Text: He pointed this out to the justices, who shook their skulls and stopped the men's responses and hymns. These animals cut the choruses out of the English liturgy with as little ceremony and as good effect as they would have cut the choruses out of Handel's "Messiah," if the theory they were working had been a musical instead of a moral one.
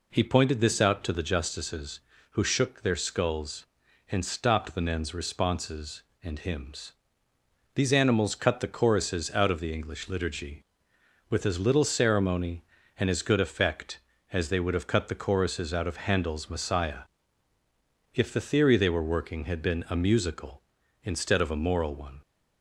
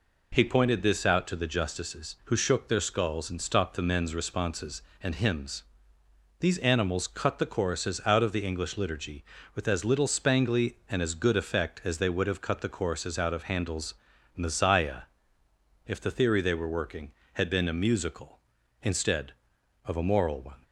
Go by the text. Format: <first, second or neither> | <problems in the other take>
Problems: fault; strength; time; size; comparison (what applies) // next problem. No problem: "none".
first | says "spangly" for "ceremony"; at 10.0 s // pauses between "Handel's" and "Messiah"; at 13.9 s; 0.42 s long